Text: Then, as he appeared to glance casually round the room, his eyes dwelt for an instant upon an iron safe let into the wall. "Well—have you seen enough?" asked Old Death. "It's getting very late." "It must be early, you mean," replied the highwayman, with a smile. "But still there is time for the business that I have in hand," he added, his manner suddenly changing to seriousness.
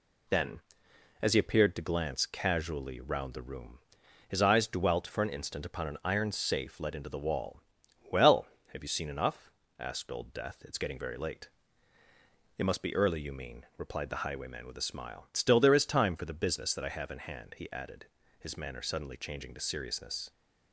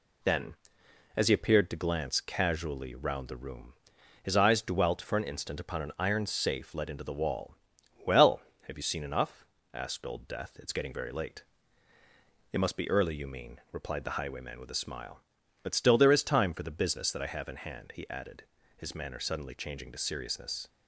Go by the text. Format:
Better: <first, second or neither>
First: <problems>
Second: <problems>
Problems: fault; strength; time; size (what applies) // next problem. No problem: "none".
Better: second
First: skips "But"; at 15.3 s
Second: none